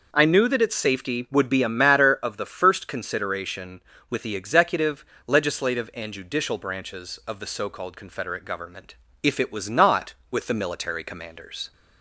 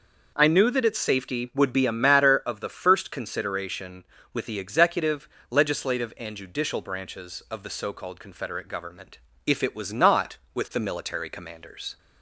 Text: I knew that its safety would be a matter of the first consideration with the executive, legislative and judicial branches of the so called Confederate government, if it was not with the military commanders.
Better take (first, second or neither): neither